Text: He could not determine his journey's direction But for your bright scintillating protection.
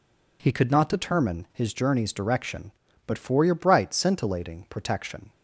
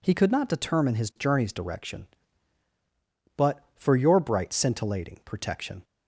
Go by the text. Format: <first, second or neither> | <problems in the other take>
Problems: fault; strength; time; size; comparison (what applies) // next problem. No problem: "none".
neither | none